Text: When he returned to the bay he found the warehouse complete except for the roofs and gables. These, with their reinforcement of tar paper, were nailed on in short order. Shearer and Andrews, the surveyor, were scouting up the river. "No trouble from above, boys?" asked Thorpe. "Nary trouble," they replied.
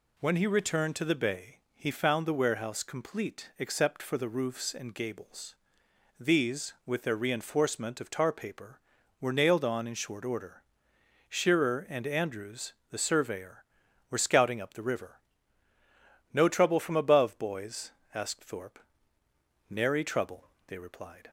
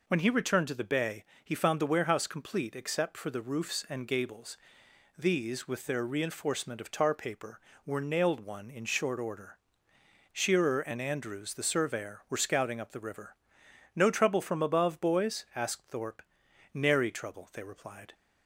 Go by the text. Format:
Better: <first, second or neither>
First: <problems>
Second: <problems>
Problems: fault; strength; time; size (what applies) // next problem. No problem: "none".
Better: first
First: pauses between "bay" and "he"; slight; at 1.5 s; 0.16 s long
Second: pauses between "bay" and "he"; slight; at 1.2 s; 0.20 s long // says "one" for "on"; at 8.3 s